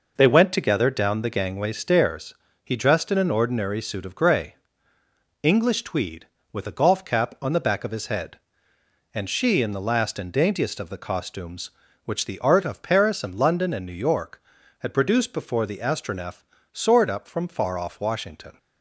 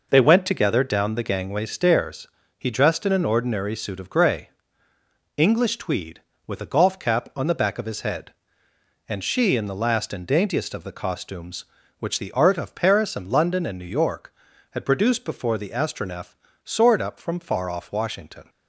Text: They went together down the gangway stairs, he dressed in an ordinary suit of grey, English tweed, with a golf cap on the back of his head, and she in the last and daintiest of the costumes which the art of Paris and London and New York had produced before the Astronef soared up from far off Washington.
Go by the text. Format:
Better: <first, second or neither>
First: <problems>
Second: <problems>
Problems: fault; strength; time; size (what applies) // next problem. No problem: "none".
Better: neither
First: pauses between "Astronef" and "soared"; slight; at 16.4 s; 0.28 s long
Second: pauses between "Astronef" and "soared"; slight; at 16.3 s; 0.28 s long